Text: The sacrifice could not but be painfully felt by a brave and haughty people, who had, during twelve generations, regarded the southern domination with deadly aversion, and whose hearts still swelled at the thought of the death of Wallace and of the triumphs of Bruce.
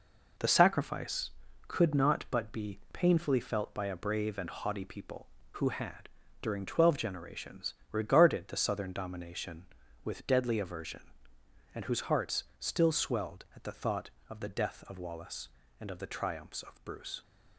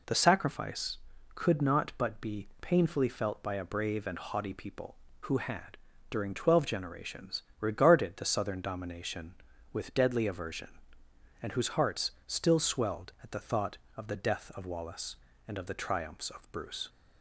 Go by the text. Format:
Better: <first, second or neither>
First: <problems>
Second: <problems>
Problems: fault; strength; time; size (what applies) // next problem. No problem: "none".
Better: second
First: gets quieter; throughout; 7 dB // pauses between "hearts" and "still"; slight; at 12.4 s; 0.16 s long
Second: pauses between "hearts" and "still"; slight; at 12.1 s; 0.16 s long